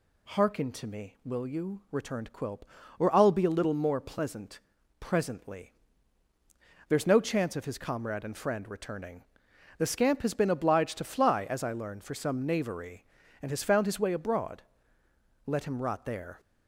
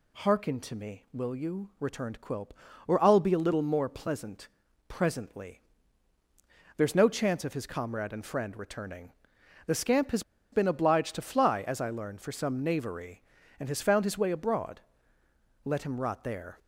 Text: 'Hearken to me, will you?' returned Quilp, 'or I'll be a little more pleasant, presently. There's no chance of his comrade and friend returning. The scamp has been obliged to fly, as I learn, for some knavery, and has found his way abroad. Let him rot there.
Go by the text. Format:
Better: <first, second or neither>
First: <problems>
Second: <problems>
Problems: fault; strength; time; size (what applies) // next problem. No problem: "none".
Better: first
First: none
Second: pauses between "has" and "been"; slight; at 10.2 s; 0.30 s long